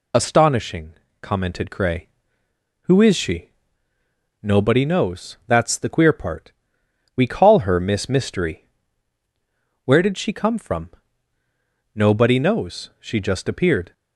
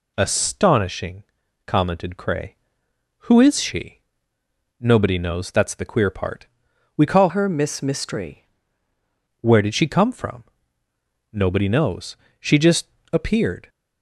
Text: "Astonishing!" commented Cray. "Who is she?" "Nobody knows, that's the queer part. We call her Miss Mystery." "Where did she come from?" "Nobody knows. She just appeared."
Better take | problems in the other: first | changes voice from "her" to "Mystery"; from 7.2 to 8.4 s; 1.2 s long // pauses between "just" and "appeared"; slight; at 12.8 s; 0.24 s long

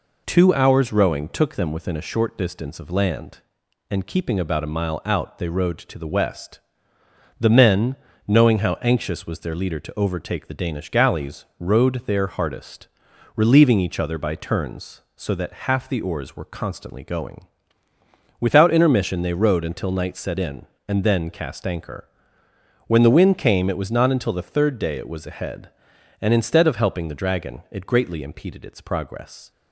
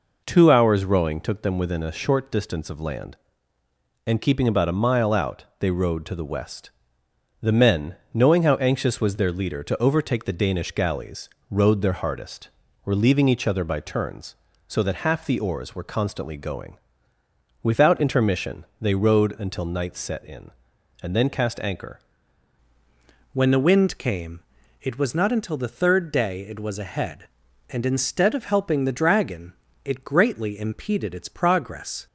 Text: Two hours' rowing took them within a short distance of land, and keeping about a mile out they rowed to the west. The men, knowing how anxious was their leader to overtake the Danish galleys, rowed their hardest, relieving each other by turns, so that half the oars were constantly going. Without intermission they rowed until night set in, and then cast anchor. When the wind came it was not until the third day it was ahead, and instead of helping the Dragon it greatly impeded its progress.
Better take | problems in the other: first | pauses between "intermission" and "they"; slight; at 18.6 s; 0.16 s long // changes voice at "When"; from 23.3 s on; 8.7 s long // pauses between "came" and "it"; at 24.4 s; 0.38 s long // pauses between "Dragon" and "it"; slight; at 29.5 s; 0.32 s long

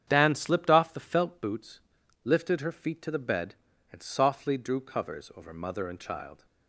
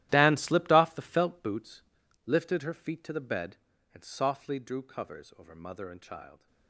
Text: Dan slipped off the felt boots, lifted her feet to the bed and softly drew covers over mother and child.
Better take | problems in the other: first | gets quieter; strong; throughout; 16 dB // starts louder than the rest; strong; until 1.1 s; 14 dB; strong in the first

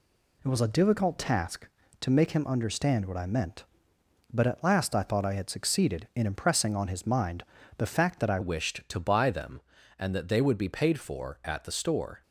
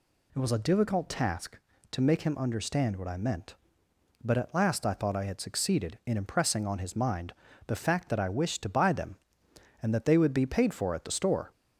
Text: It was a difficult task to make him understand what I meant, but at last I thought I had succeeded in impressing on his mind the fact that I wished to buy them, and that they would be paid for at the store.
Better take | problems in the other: second | pauses between "mind" and "the"; slight; at 7.4 s; 0.34 s long; slight in the second // changes voice at "wished"; from 8.4 s on; 3.8 s long

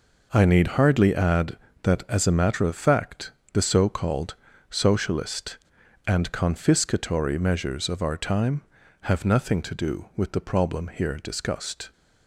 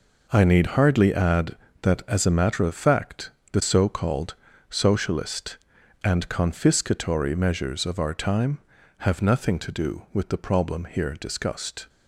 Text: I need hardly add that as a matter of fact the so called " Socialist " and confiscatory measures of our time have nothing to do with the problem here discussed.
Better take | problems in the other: neither | pauses between "fact" and "the"; slight; the same in both

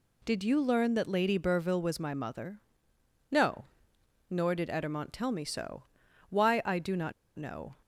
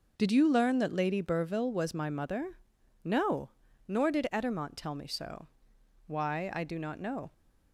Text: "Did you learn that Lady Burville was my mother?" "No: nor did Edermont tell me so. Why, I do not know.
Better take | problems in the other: second | pauses between "not" and "know"; slight; at 7.1 s; 0.23 s long

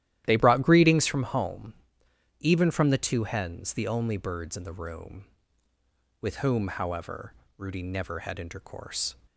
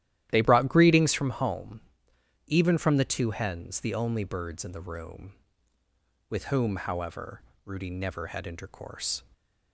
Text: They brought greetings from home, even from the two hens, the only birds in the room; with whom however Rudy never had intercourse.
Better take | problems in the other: neither | starts louder than the rest; strong; the same in both // pauses between "however" and "Rudy"; slight; the same in both

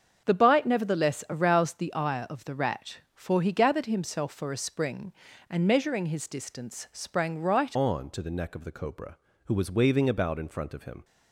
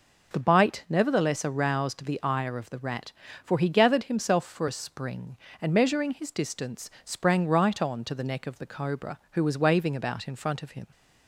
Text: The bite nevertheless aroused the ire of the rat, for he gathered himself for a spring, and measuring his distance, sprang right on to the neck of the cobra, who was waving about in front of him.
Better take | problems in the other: second | starts louder than the rest; until 1.2 s; 7 dB // changes voice at "on"; from 7.7 s on; 3.3 s long

